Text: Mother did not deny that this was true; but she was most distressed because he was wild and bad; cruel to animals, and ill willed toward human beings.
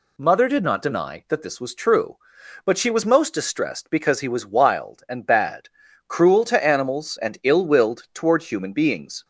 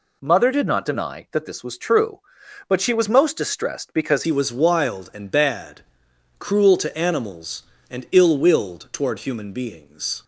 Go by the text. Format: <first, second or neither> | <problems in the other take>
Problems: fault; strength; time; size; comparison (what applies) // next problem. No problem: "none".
first | changes voice at "he"; from 4.2 s on; 6.0 s long